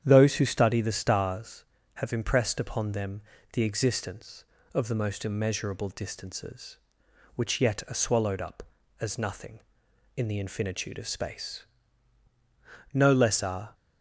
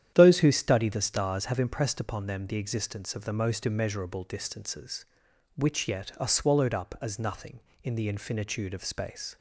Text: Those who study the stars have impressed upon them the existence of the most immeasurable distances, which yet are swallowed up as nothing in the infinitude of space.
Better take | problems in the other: second | starts louder than the rest; strong; until 1.0 s; 9.5 dB; strong in the second // pauses between "them" and "the"; slight; at 3.2 s; 0.30 s long // goes on to say "No less are"; noticeable; from 12.9 s on; 0.82 s long

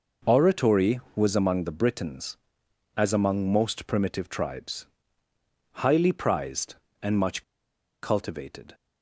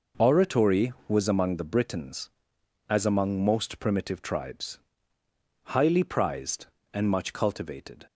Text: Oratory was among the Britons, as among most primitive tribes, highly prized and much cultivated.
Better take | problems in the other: second | pauses between "much" and "cultivated"; noticeable; at 7.4 s; 0.59 s long

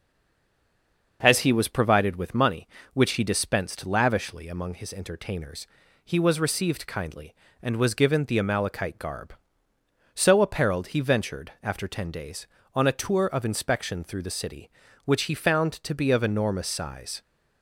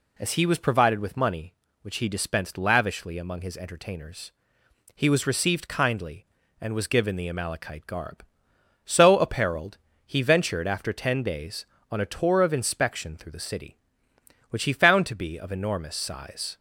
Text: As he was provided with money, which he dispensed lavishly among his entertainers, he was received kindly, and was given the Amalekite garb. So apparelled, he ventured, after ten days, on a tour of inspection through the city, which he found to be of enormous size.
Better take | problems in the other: second | stays silent before the first word; noticeable; until 1.2 s; 1.2 s long // starts louder than the rest; noticeable; until 2.2 s; 6 dB

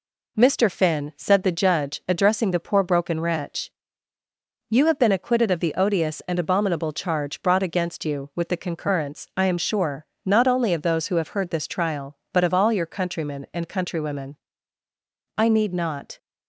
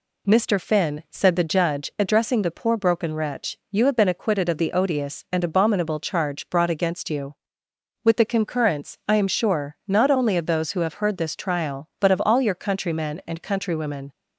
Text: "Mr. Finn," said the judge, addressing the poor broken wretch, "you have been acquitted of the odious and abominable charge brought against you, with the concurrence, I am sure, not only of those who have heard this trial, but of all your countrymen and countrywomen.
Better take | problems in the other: second | goes on to say "I need not"; noticeable; from 15.3 s on; 0.80 s long

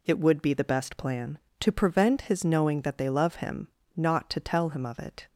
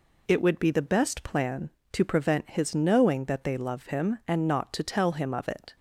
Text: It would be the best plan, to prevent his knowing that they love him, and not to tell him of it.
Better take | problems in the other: second | skips "and"; at 3.8 s

